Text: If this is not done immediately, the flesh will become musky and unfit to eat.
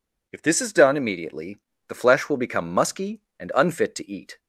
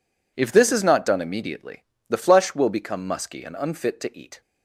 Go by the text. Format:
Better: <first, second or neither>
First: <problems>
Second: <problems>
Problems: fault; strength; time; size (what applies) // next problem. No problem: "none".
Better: second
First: skips "not"; at 0.7 s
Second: none